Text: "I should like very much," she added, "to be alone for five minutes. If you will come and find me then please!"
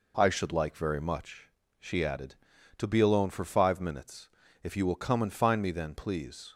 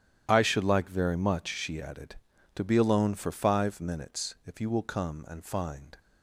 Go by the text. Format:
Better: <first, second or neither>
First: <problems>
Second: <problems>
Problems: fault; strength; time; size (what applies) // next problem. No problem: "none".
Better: first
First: none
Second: starts louder than the rest; strong; until 1.2 s; 11 dB // stops before "me then please"; at 5.9 s